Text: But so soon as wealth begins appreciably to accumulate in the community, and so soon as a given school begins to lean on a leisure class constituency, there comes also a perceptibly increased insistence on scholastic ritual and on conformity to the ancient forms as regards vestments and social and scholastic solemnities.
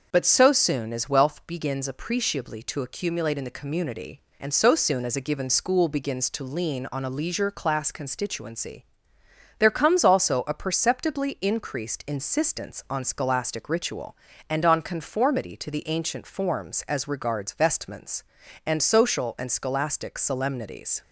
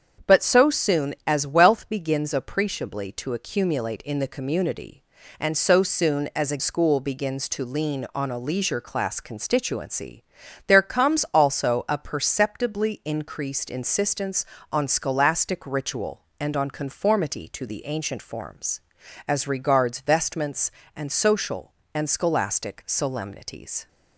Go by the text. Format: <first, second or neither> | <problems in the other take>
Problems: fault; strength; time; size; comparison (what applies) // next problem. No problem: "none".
first | starts louder than the rest; strong; until 1.3 s; 7.5 dB; noticeable in the first // skips "given"; at 6.5 s